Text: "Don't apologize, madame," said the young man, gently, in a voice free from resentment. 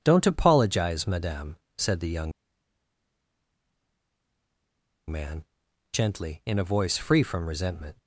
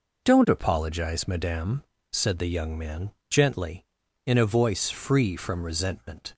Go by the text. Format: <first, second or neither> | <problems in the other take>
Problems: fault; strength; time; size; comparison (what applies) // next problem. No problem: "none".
second | pauses between "young" and "man"; strong; at 2.3 s; 2.7 s long